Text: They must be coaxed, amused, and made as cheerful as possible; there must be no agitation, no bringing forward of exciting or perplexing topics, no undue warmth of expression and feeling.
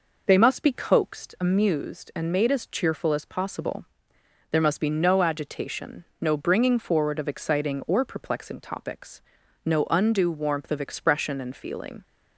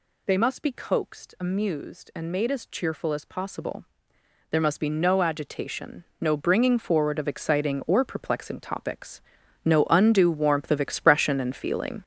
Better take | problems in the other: first | gets louder; strong; throughout; 7.5 dB

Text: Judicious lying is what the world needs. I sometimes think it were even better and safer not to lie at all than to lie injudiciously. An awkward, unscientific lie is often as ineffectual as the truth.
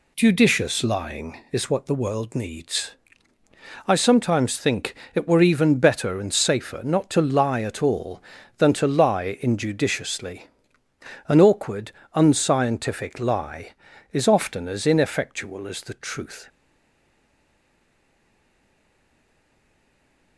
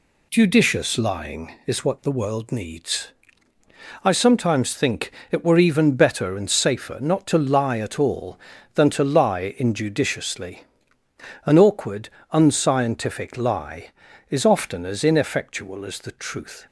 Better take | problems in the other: second | pauses between "think" and "it"; slight; at 4.9 s; 0.18 s long; slight in the second // stays silent after the last word; strong; from 16.4 s on; 3.9 s long

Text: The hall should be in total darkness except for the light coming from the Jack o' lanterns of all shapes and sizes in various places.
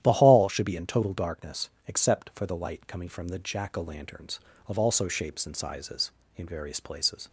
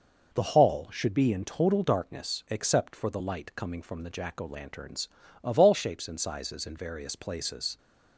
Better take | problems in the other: second | starts louder than the rest; strong; until 1.0 s; 11.5 dB // pauses between "darkness" and "except"; slight; at 1.6 s; 0.18 s long // says "also" for "all"; at 4.7 s

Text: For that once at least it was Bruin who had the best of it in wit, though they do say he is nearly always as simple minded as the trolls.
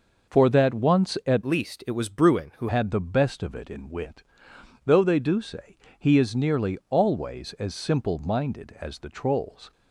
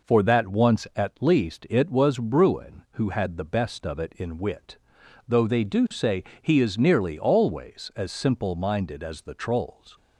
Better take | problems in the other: second | changes voice from "least" to "who"; from 1.4 to 2.6 s; 1.2 s long // pauses between "say" and "he"; slight; at 5.7 s; 0.20 s long; slight in the second

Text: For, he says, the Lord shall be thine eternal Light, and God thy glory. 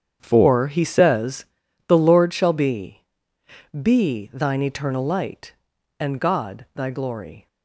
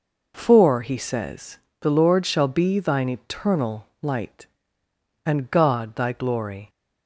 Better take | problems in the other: second | starts louder than the rest; strong; until 1.2 s; 8.5 dB // says "be" twice; at 3.8 s

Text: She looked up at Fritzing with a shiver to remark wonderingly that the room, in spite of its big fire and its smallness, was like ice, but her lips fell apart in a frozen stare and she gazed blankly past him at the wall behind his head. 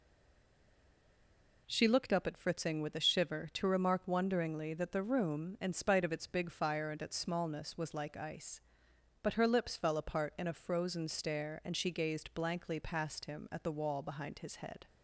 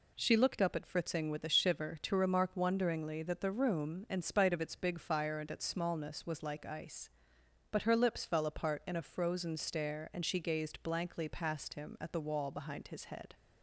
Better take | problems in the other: second | stays silent before the first word; noticeable; until 1.6 s; 1.6 s long

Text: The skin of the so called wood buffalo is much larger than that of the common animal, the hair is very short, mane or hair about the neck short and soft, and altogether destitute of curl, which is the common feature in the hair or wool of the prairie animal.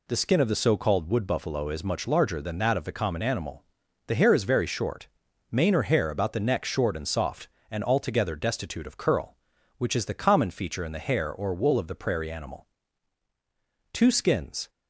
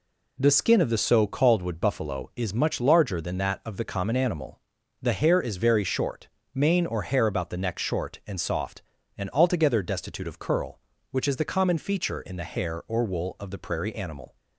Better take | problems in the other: second | goes on to say "Two skins"; noticeable; from 13.9 s on; 0.78 s long

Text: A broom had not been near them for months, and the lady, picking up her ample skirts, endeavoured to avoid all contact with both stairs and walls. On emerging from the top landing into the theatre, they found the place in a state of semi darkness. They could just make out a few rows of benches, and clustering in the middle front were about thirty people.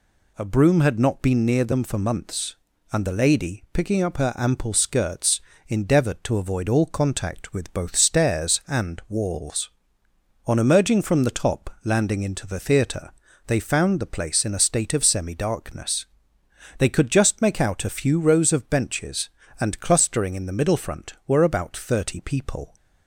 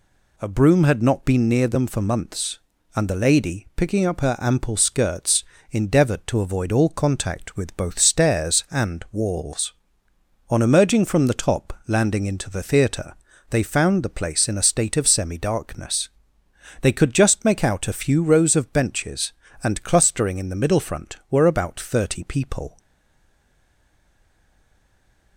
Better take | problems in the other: first | pauses between "top" and "landing"; slight; at 11.7 s; 0.16 s long; slight in the first // stays silent after the last word; strong; from 22.7 s on; 2.6 s long

